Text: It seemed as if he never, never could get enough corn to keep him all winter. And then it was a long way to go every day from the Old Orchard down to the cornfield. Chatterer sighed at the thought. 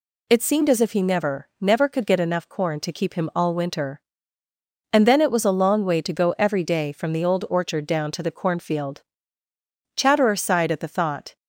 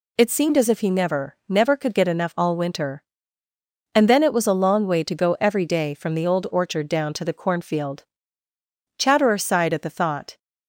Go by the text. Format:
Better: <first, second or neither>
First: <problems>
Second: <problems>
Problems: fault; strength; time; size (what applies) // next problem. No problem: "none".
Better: first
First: none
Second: skips "corn to keep him"; at 2.3 s